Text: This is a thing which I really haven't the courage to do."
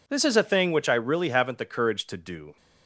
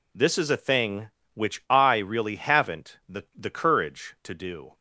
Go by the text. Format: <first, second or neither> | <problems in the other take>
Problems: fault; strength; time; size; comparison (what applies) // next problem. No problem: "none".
first | says "the" twice; at 3.3 s